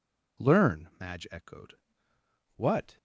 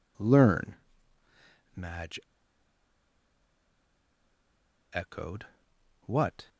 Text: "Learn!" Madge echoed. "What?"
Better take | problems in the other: first | pauses between "Madge" and "echoed"; strong; at 2.2 s; 2.7 s long

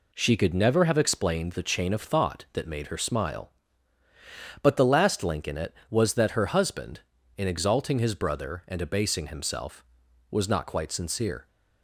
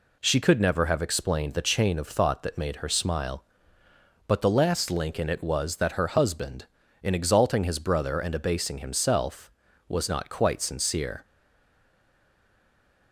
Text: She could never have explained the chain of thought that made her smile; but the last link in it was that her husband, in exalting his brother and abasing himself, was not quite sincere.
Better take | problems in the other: first | stays silent after the last word; noticeable; from 11.2 s on; 1.9 s long

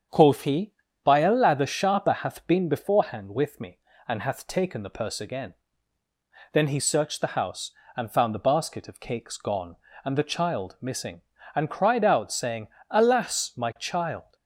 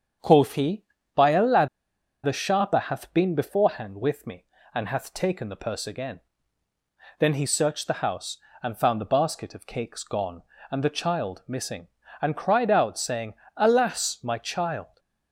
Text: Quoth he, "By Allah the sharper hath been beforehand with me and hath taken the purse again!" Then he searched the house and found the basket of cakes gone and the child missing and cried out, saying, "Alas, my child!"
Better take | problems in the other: first | starts louder than the rest; strong; until 1.5 s; 7.5 dB; strong in the first // pauses between "Allah" and "the"; noticeable; at 1.6 s; 0.57 s long

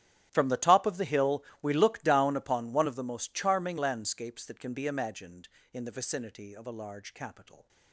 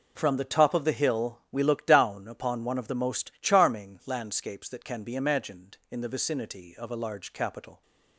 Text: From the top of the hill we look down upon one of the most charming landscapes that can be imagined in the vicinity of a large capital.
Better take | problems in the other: second | gets quieter; strong; throughout; 19 dB // pauses between "hill" and "we"; slight; at 1.4 s; 0.18 s long

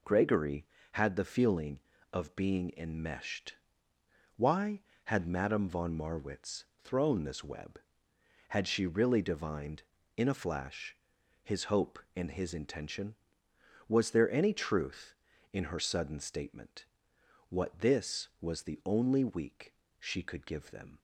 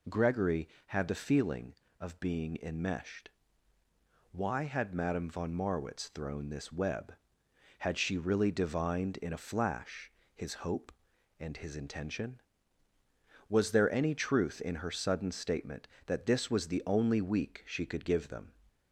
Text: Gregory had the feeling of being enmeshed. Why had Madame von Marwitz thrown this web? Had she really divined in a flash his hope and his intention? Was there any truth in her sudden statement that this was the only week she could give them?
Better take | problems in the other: second | pauses between "Marwitz" and "thrown"; slight; at 6.6 s; 0.18 s long // pauses between "flash" and "his"; noticeable; at 10.9 s; 0.48 s long; slight in the second // says "what" for "that"; at 17.4 s // pauses between "week" and "she"; slight; at 19.7 s; 0.24 s long

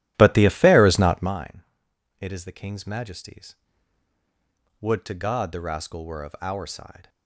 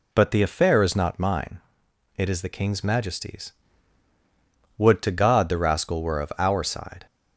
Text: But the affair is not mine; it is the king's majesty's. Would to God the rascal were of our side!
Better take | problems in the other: second | starts louder than the rest; strong; until 1.4 s; 14 dB

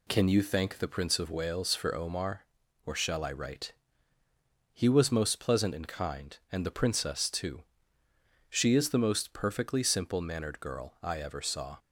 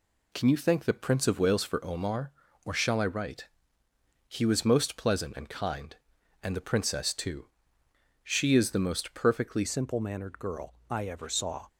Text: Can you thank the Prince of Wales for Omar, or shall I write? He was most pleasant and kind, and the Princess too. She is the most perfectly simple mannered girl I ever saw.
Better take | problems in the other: first | changes voice at "simple"; from 9.6 s on; 2.0 s long

